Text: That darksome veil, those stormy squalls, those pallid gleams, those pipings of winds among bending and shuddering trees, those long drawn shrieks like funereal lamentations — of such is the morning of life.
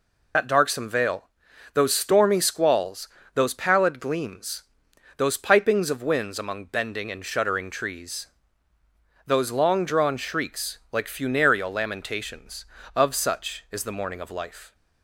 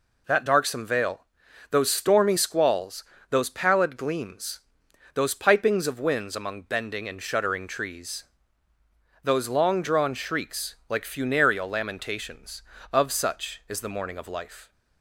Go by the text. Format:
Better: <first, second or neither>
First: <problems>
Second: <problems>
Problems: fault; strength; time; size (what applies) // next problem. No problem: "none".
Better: second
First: loses the start of "That"; at 0.3 s; 70 ms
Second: none